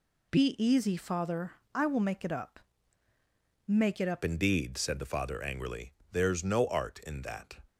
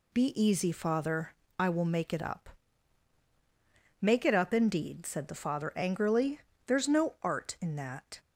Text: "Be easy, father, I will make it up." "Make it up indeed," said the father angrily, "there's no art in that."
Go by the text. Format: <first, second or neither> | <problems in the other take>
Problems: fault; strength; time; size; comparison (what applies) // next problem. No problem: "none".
second | changes voice at "indeed"; from 4.2 s on; 3.3 s long